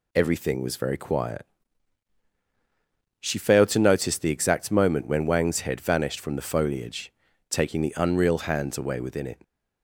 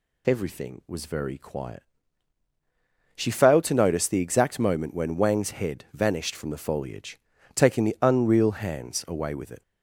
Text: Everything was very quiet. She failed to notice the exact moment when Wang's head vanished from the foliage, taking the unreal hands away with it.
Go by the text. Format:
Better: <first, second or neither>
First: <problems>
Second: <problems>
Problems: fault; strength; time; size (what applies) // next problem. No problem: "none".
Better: second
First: says "within" for "with"; at 8.9 s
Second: none